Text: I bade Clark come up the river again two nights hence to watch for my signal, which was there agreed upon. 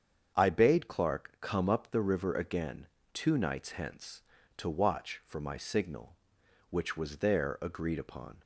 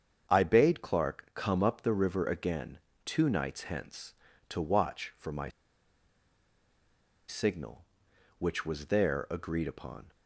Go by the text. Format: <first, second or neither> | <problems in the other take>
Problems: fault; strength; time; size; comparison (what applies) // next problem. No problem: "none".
first | starts louder than the rest; strong; until 1.3 s; 7.5 dB; strong in the first // pauses between "again" and "two"; slight; at 2.7 s; 0.26 s long; slight in the first // pauses between "my" and "signal"; strong; at 5.4 s; 1.7 s long